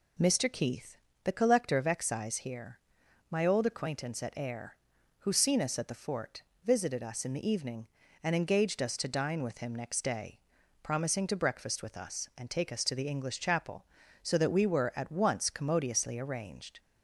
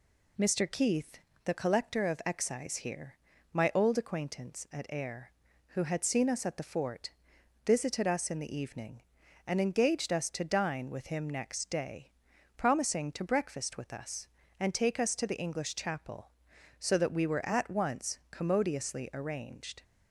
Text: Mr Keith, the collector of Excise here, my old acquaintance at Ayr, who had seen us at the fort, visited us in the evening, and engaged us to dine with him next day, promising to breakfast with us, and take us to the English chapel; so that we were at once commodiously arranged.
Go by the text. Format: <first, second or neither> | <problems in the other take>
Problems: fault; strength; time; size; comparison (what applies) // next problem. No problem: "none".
second | skips "had"; at 5.3 s